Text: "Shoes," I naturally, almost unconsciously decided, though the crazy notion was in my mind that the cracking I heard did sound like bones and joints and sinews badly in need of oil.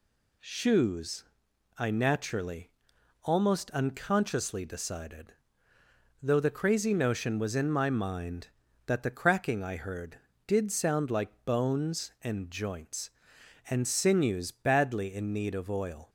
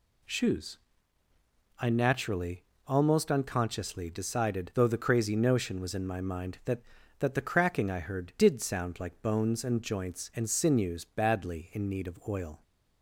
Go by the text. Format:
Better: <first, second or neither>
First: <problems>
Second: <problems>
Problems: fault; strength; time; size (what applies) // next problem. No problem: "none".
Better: first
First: none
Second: says "that" twice; at 7.1 s